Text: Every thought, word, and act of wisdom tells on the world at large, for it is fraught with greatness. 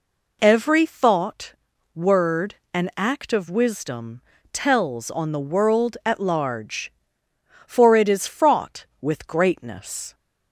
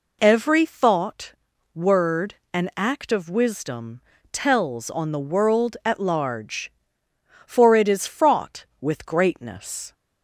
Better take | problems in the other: neither | pauses between "wisdom" and "tells"; slight; the same in both

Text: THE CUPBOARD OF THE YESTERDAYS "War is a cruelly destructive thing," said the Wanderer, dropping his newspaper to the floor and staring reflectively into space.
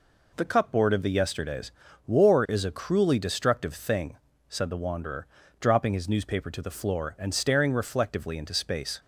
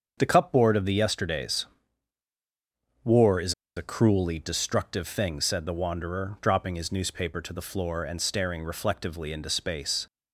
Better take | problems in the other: first | starts louder than the rest; until 1.2 s; 7 dB // pauses between "YESTERDAYS" and "War"; strong; at 1.6 s; 1.3 s long; slight in the first // pauses between "is" and "a"; slight; at 3.5 s; 0.23 s long

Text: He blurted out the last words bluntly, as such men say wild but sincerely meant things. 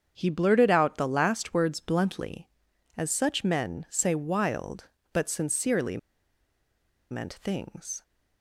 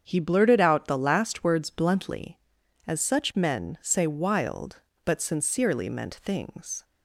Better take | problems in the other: second | starts louder than the rest; strong; until 1.1 s; 7.5 dB; strong in the second // pauses between "sincerely" and "meant"; at 5.9 s; 1.1 s long

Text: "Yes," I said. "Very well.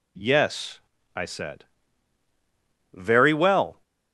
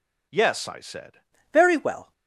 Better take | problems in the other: first | changes voice at "Very"; from 1.5 s on; 0.6 s long

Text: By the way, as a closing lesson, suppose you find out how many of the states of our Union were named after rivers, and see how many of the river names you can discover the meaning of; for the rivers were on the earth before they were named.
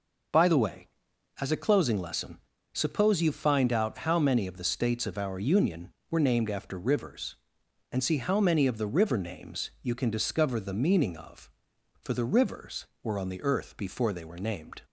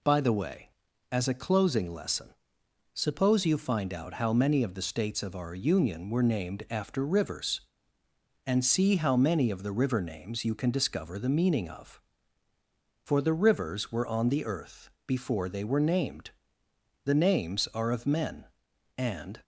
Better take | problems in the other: first | pauses between "earth" and "before"; slight; at 14.8 s; 0.16 s long // goes on to say "The names are of men and"; strong; from 17.0 s on; 2.4 s long

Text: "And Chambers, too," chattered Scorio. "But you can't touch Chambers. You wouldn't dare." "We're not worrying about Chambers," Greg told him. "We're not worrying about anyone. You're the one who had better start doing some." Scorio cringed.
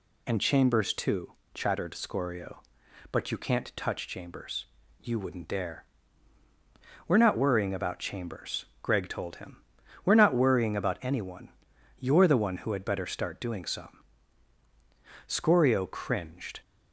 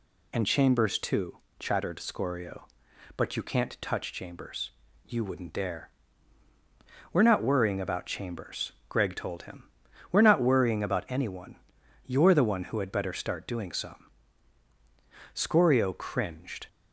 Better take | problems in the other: neither | none

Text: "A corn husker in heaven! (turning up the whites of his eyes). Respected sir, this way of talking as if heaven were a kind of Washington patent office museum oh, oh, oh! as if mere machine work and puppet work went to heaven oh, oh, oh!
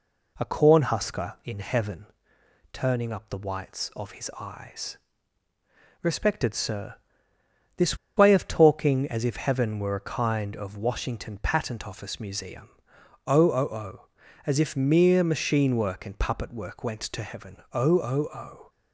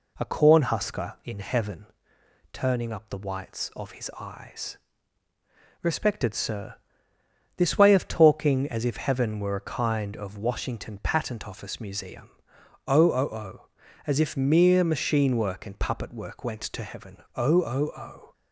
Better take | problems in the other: second | pauses between "this" and "way"; slight; at 7.9 s; 0.20 s long // pauses between "museum" and "oh"; noticeable; at 12.6 s; 0.56 s long; noticeable in the second // pauses between "heaven" and "oh"; slight; at 17.5 s; 0.16 s long; slight in the second

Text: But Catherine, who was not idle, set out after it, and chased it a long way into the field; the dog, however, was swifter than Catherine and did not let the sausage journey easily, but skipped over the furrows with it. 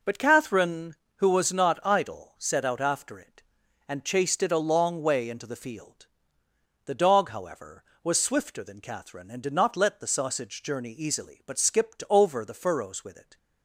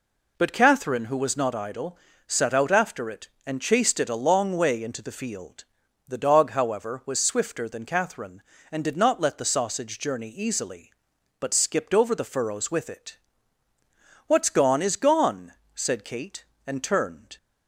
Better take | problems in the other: first | goes on to say "What's gone is gone said Kate and turned"; strong; from 14.2 s on; 3.1 s long

